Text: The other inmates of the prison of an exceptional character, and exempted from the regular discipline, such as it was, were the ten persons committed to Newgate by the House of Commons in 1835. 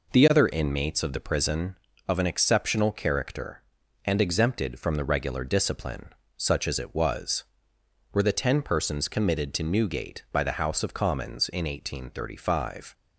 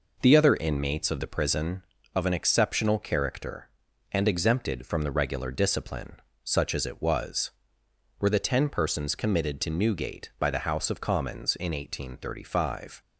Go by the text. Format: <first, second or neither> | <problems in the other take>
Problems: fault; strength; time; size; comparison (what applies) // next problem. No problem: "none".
neither | none